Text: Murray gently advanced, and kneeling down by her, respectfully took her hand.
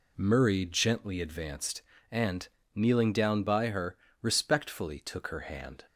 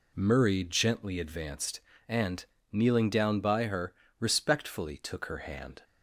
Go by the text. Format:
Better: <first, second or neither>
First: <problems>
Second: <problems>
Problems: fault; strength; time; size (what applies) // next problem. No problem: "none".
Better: neither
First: pauses between "and" and "kneeling"; slight; at 2.4 s; 0.26 s long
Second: pauses between "and" and "kneeling"; slight; at 2.4 s; 0.26 s long